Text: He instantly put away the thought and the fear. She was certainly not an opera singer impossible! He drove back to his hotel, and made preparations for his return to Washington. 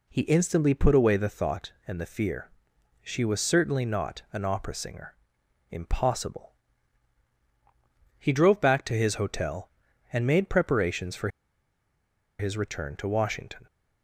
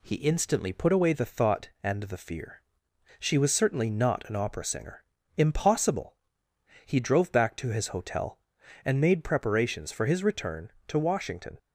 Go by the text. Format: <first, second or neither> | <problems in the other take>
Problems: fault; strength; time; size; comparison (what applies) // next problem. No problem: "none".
second | pauses between "singer" and "impossible"; noticeable; at 5.1 s; 0.56 s long; slight in the second // pauses between "for" and "his"; at 11.2 s; 1.1 s long